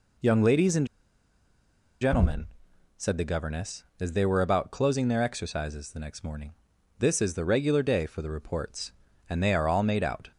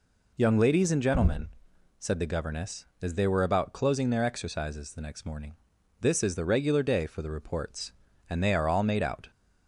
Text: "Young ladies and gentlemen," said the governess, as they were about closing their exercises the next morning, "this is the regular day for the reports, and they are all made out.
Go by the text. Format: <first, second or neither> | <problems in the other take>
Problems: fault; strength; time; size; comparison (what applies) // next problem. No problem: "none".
second | pauses between "and" and "gentlemen"; at 0.8 s; 1.1 s long